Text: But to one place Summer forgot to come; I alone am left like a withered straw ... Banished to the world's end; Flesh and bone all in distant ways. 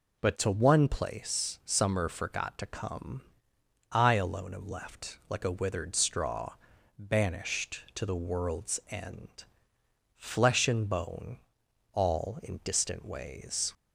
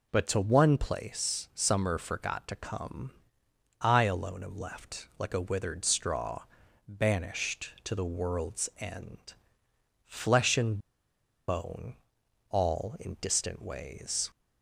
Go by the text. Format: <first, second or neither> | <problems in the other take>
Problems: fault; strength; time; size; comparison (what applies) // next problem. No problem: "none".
first | pauses between "and" and "bone"; noticeable; at 10.7 s; 0.69 s long // pauses between "bone" and "all"; noticeable; at 11.9 s; 0.54 s long; noticeable in the first